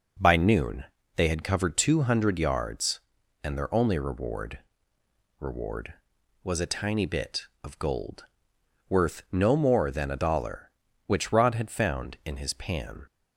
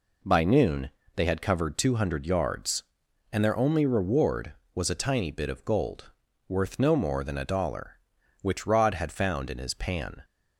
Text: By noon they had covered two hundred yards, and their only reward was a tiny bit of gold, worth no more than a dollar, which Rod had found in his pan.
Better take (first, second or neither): second